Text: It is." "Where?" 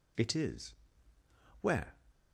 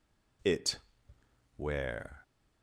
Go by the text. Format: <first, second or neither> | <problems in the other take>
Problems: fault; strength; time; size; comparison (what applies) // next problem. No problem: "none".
first | skips "is"; at 1.1 s